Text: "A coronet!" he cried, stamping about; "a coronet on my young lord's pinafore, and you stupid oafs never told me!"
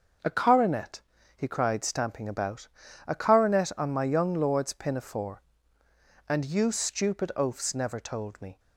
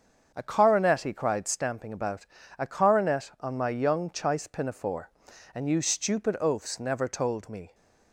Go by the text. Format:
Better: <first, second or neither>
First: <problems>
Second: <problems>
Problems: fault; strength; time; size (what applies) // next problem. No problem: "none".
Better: first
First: starts louder than the rest; until 1.6 s; 6.5 dB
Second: starts louder than the rest; until 1.3 s; 7 dB // says "chice" for "lord's"; at 4.0 s